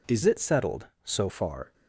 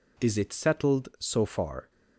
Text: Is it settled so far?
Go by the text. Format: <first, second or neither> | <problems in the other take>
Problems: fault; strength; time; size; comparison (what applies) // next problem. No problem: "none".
second | changes voice from "it" to "so"; from 0.2 to 1.2 s; 1.0 s long